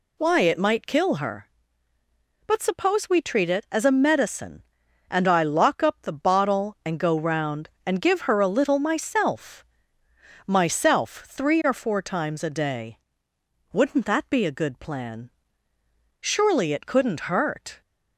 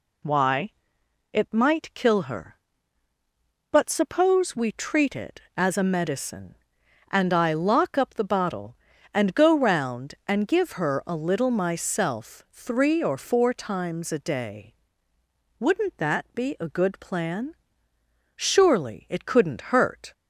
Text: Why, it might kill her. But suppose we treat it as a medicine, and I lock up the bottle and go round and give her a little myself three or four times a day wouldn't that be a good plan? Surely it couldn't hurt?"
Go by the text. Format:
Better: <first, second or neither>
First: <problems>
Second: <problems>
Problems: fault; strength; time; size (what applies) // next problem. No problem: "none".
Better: second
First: says "myself" twice; at 10.4 s // pauses between "day" and "wouldn't"; noticeable; at 12.9 s; 0.74 s long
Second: pauses between "day" and "wouldn't"; noticeable; at 14.7 s; 0.84 s long